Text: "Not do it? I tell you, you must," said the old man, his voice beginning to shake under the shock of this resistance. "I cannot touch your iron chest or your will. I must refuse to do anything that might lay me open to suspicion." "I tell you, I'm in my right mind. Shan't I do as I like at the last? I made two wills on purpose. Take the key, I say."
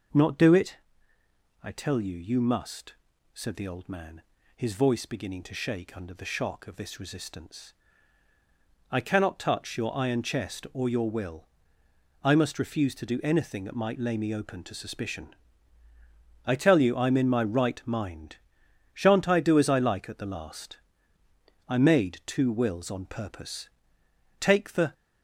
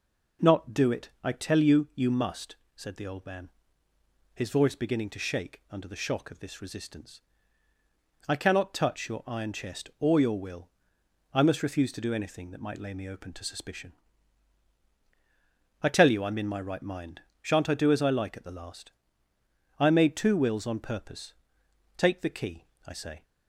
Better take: second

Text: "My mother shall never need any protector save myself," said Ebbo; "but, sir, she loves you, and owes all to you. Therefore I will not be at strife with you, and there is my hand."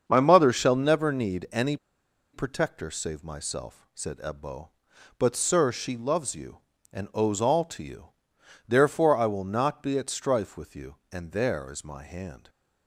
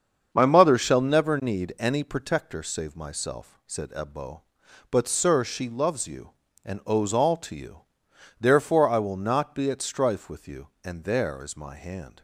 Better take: second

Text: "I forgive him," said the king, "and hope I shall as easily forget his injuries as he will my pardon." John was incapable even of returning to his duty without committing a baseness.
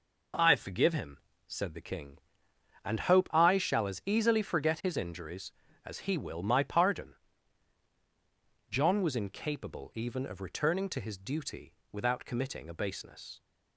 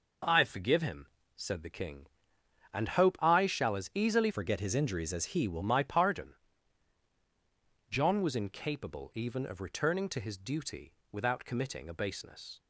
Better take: first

